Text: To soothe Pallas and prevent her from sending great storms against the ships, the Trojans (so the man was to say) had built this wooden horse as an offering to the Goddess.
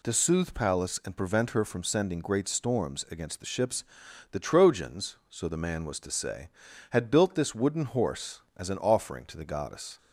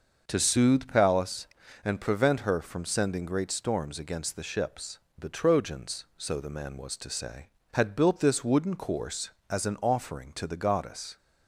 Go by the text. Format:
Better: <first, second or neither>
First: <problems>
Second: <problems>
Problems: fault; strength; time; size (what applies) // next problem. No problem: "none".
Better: first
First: none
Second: starts louder than the rest; until 1.2 s; 6 dB // says "course" for "horse"; at 8.7 s